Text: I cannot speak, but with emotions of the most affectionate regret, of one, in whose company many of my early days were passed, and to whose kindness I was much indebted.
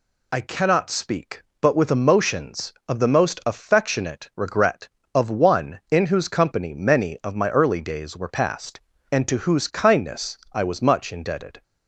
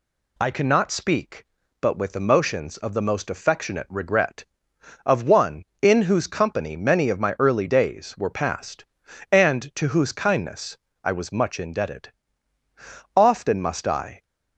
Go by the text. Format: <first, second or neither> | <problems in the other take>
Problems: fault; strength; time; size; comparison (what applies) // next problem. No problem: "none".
first | pauses between "kindness" and "I"; slight; at 10.7 s; 0.28 s long; slight in the first // goes on to say "Often must I"; noticeable; from 13.1 s on; 1.0 s long